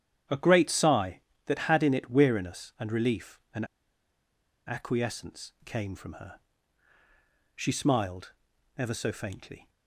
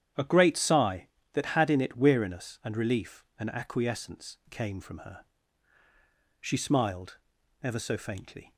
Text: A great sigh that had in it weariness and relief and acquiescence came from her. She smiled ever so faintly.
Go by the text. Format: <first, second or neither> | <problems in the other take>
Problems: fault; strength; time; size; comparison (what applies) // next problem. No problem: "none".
second | starts louder than the rest; strong; until 1.5 s; 10 dB; strong in the second // pauses between "and" and "acquiescence"; at 3.6 s; 1.0 s long // pauses between "smiled" and "ever"; at 8.3 s; 0.44 s long; also in the second